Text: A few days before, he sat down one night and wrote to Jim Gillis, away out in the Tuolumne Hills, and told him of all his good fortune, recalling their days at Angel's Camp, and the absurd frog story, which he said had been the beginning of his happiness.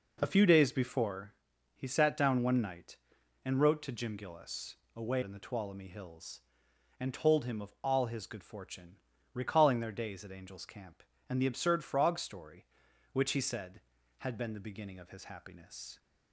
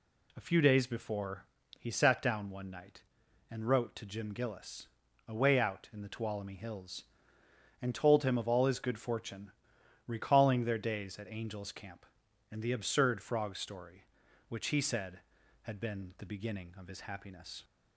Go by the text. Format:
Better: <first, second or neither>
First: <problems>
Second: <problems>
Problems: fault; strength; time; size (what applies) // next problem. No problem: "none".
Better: second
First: skips "out"; at 5.2 s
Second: none